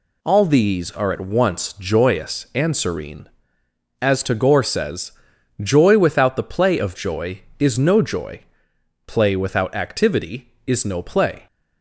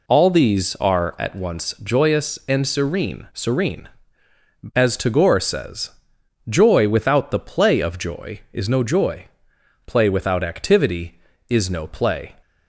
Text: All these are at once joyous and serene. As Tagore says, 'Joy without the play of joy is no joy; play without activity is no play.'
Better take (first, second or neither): first